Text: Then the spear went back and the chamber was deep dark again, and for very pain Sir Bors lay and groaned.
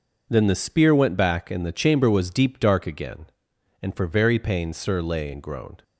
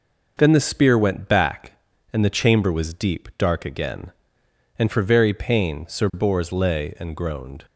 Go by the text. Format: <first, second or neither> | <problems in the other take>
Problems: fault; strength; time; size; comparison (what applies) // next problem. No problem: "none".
second | skips "Bors"; at 4.9 s